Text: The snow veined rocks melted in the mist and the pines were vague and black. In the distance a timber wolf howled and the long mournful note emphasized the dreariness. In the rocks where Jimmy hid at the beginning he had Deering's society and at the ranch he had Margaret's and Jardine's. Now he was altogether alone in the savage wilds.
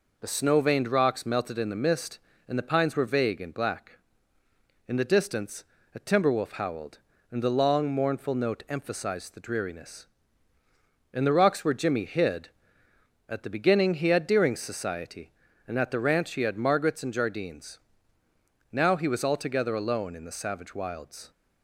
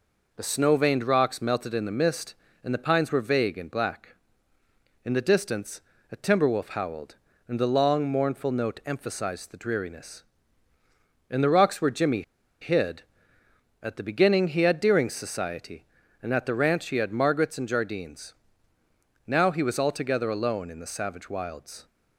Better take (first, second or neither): first